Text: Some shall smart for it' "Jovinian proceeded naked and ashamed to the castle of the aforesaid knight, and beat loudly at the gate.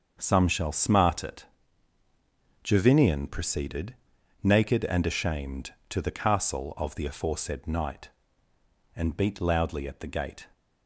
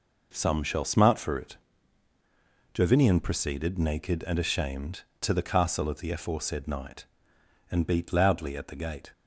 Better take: second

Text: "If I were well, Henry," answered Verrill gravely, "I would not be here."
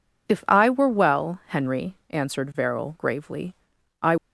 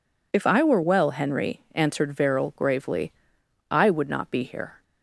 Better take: second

